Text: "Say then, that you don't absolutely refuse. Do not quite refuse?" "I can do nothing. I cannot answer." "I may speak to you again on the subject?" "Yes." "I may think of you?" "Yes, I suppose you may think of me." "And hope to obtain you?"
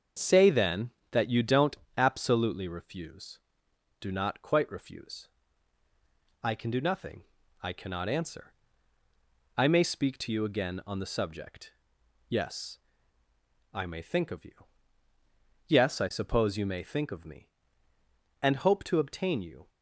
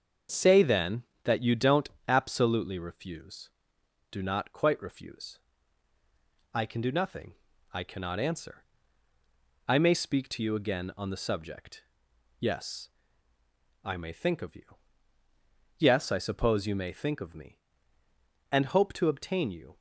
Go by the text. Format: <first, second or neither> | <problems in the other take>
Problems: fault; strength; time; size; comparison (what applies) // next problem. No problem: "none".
neither | starts louder than the rest; the same in both // pauses between "don't" and "absolutely"; slight; the same in both